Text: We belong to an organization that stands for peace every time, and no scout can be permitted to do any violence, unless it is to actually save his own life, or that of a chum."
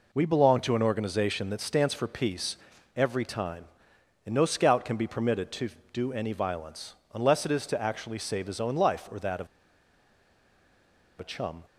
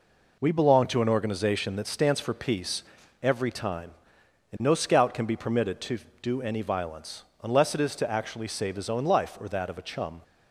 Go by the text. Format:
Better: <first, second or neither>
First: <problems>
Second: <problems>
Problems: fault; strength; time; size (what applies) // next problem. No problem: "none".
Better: second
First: pauses between "peace" and "every"; at 2.5 s; 0.38 s long // pauses between "of" and "a"; strong; at 9.4 s; 1.7 s long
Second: pauses between "peace" and "every"; at 2.8 s; 0.38 s long